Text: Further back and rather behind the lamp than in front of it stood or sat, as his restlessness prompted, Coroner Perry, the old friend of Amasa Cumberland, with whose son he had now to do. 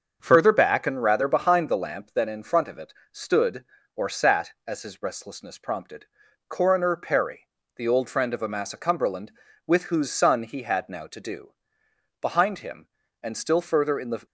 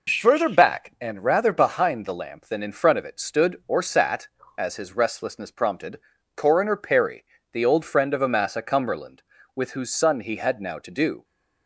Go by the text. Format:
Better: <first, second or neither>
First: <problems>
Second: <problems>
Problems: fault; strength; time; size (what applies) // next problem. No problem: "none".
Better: second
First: starts louder than the rest; until 1.2 s; 6.5 dB // pauses between "it" and "stood"; slight; at 2.9 s; 0.18 s long // goes on to say "Behind him and still further in the"; strong; from 12.2 s on; 2.0 s long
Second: none